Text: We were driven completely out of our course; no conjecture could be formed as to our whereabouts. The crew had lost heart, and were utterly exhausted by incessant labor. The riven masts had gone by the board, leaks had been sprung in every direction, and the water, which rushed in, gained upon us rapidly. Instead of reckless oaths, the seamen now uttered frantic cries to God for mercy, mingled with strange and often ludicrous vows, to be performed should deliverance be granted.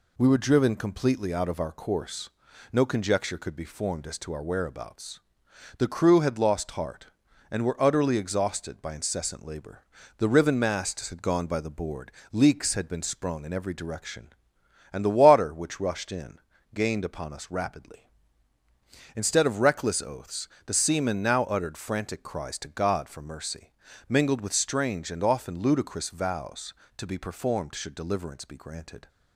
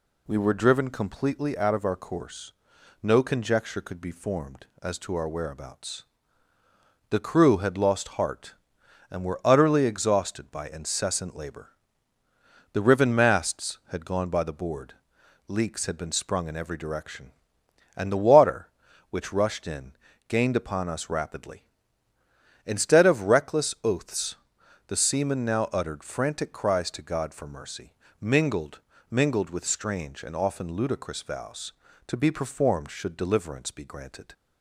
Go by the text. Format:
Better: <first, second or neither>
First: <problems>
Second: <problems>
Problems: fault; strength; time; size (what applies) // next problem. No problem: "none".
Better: first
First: none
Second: says "mingled" twice; at 29.0 s